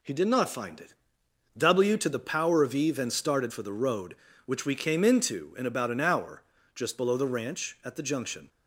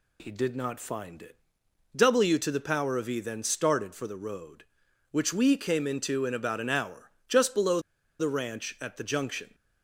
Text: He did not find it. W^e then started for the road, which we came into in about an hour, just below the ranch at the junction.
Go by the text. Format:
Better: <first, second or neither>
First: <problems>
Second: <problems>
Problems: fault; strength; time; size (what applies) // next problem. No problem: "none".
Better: first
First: none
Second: pauses between "below" and "the"; at 7.8 s; 0.38 s long